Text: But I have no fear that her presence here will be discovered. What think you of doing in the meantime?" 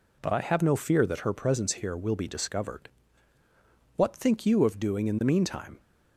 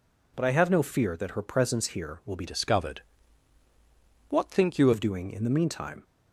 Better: first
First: none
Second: changes voice from "discovered" to "you"; from 2.4 to 4.9 s; 2.5 s long

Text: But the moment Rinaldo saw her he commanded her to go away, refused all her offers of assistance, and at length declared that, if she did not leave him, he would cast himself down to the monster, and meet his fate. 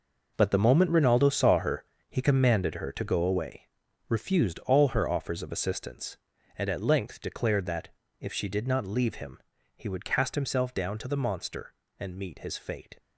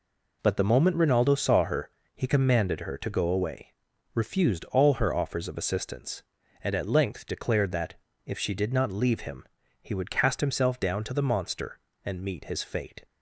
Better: second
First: gets quieter; strong; throughout; 11.5 dB // pauses between "her" and "he"; slight; at 1.8 s; 0.26 s long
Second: pauses between "her" and "he"; slight; at 1.8 s; 0.26 s long

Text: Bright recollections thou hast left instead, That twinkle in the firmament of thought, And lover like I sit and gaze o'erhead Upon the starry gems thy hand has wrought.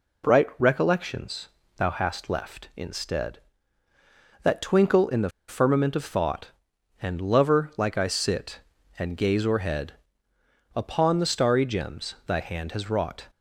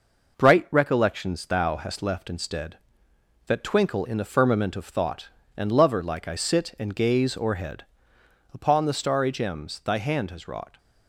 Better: second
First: pauses between "recollections" and "thou"; slight; at 1.4 s; 0.28 s long // pauses between "the" and "firmament"; slight; at 5.2 s; 0.19 s long // pauses between "o'erhead" and "Upon"; noticeable; at 9.9 s; 0.82 s long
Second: pauses between "o'erhead" and "Upon"; noticeable; at 7.8 s; 0.70 s long

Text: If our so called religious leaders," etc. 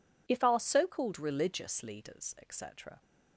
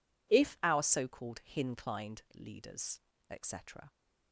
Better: first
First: none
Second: says "hinclined" for "religious"; at 1.4 s

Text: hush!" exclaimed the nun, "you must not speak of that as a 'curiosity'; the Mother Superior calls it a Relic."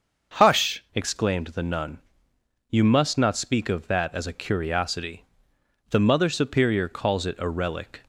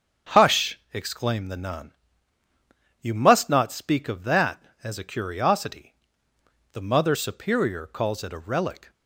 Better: second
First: starts louder than the rest; until 1.4 s; 6 dB // changes voice at "exclaimed"; from 0.9 s on; 7.1 s long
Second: starts louder than the rest; strong; until 1.4 s; 7 dB

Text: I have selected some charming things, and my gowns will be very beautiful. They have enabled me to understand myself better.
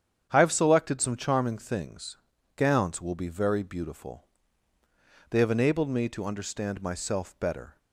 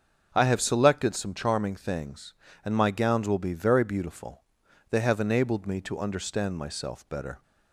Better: second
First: starts louder than the rest; strong; until 1.3 s; 8.5 dB // skips "and my"; at 2.3 s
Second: starts louder than the rest; until 1.3 s; 6.5 dB

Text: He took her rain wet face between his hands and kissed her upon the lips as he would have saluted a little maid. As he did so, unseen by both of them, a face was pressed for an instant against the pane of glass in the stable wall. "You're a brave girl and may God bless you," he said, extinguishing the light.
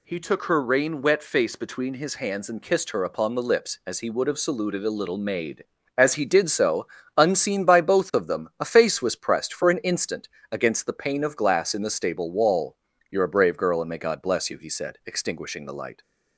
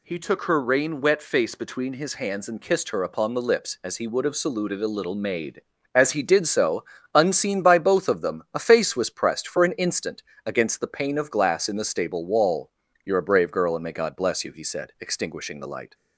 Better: neither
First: pauses between "instant" and "against"; slight; at 10.2 s; 0.24 s long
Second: pauses between "instant" and "against"; slight; at 10.2 s; 0.24 s long

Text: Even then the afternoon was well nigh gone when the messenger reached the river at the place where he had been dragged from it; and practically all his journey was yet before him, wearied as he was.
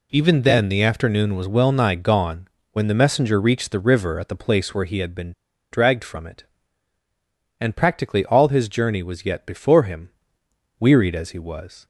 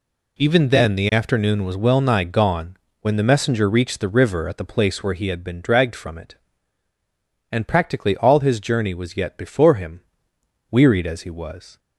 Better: second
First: pauses between "gone" and "when"; slight; at 2.4 s; 0.24 s long // pauses between "been" and "dragged"; at 5.3 s; 0.40 s long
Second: pauses between "gone" and "when"; slight; at 2.7 s; 0.24 s long

